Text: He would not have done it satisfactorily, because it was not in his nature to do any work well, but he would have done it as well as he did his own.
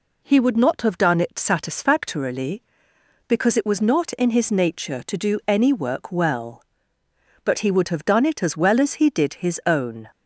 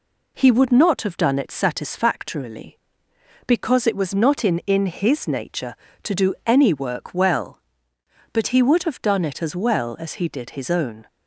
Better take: first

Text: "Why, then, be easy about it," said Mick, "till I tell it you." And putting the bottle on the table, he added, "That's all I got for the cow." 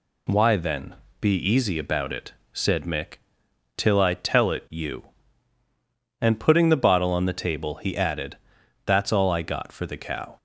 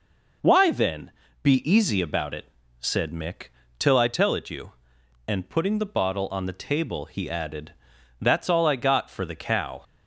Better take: neither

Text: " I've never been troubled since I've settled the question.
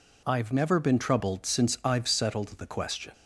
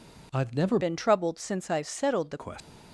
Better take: first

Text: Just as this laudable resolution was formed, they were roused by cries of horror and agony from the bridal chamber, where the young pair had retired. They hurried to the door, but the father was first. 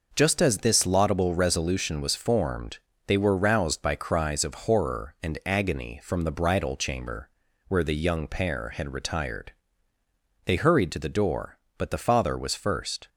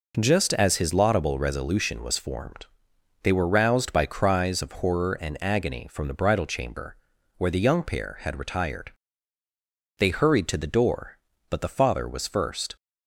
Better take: first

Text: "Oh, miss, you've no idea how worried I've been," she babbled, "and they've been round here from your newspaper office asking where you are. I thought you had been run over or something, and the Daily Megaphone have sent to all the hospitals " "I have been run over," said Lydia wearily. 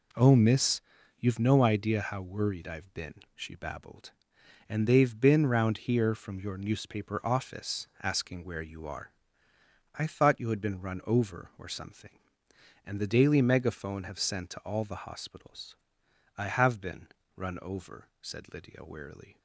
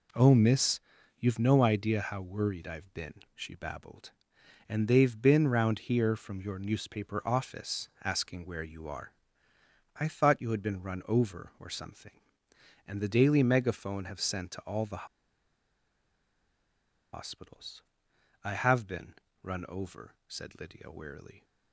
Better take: first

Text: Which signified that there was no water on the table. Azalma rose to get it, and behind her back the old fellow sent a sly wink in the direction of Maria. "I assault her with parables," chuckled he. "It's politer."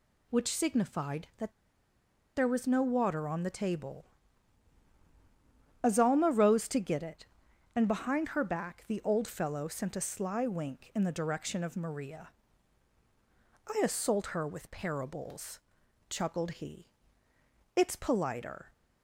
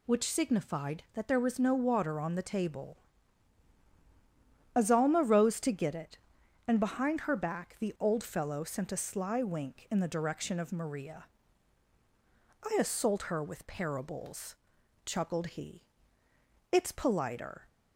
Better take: second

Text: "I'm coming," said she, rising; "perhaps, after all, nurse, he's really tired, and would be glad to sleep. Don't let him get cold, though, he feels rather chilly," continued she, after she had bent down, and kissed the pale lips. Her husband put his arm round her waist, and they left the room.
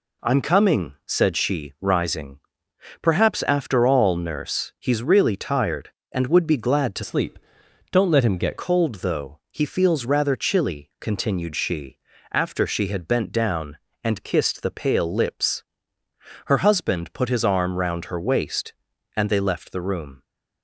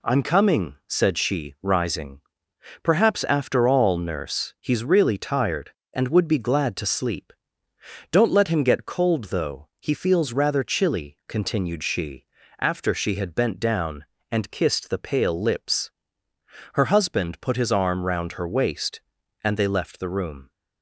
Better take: second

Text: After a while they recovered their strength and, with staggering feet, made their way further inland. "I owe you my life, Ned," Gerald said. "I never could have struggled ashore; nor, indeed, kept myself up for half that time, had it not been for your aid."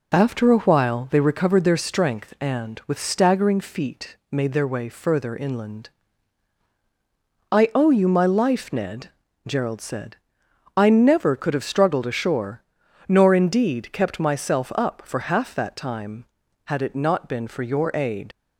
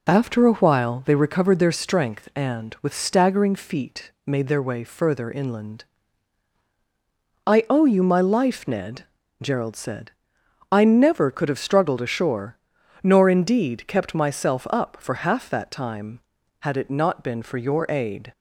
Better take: second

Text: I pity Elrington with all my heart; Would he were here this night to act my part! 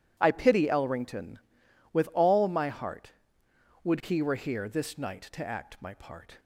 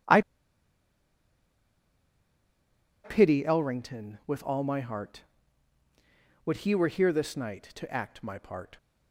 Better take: first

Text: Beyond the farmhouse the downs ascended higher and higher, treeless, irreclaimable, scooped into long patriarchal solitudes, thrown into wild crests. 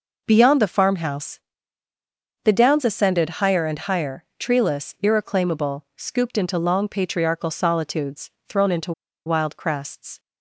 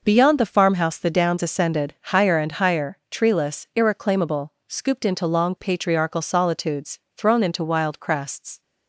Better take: second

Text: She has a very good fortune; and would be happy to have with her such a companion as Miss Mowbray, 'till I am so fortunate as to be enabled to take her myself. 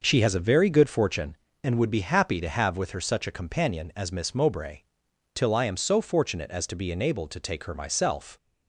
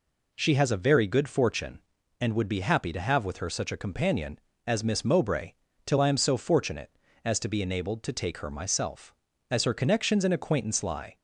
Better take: first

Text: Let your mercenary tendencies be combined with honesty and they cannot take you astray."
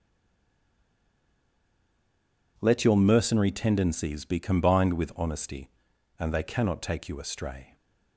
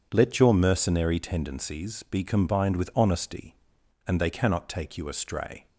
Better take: second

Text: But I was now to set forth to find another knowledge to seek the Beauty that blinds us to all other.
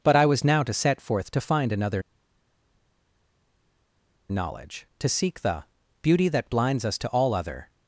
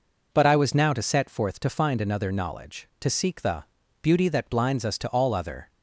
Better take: second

